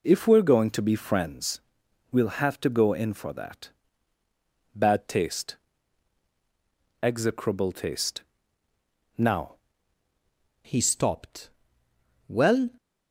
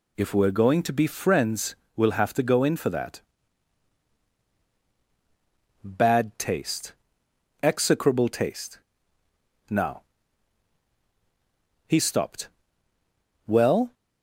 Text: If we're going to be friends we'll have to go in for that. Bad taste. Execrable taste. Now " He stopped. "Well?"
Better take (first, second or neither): second